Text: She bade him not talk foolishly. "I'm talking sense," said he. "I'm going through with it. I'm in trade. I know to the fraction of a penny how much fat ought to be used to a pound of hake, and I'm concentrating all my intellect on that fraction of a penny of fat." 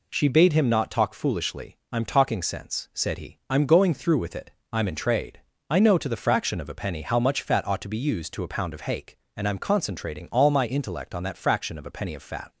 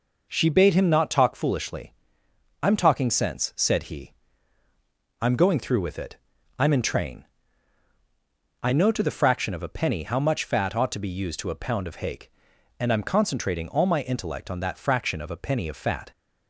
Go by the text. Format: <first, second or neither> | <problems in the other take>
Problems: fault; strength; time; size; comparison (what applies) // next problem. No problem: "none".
first | says "train" for "trade"; at 6.8 s